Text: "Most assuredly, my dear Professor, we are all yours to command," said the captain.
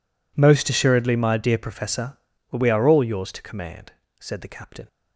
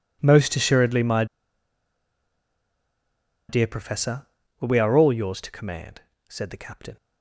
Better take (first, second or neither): first